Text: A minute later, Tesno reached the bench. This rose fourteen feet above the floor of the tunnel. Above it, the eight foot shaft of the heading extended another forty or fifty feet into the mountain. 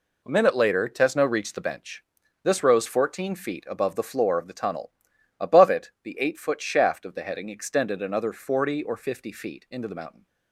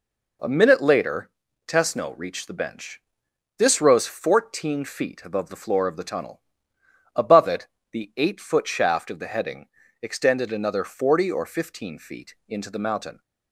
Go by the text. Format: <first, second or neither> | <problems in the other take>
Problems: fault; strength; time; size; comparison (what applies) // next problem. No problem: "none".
first | pauses between "heading" and "extended"; slight; at 9.6 s; 0.32 s long // says "fifteen" for "fifty"; at 11.4 s